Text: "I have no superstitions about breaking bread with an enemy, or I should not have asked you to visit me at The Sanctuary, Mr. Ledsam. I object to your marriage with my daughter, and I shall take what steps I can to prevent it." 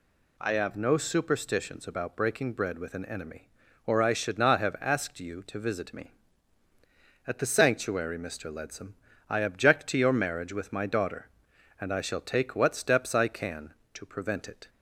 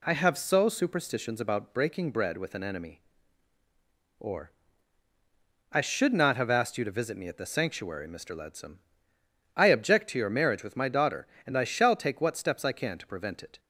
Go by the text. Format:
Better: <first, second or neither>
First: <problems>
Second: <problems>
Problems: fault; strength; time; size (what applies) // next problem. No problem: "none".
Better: first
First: none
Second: says "so" for "no"; at 0.3 s // pauses between "or" and "I"; at 4.5 s; 1.2 s long